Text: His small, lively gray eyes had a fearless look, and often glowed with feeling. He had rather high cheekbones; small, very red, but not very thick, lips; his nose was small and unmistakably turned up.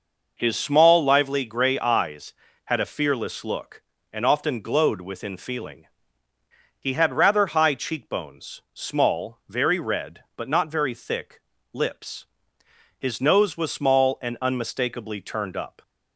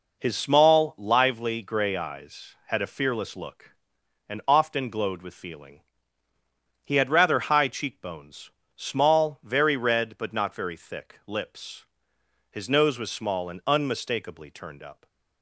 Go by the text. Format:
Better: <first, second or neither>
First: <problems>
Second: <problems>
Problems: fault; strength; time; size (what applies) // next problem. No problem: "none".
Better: second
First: says "within" for "with"; at 4.9 s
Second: none